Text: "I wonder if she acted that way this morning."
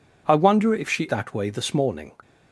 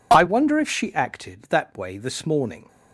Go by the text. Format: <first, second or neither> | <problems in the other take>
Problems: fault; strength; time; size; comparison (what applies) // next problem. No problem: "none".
second | skips "acted"; at 1.0 s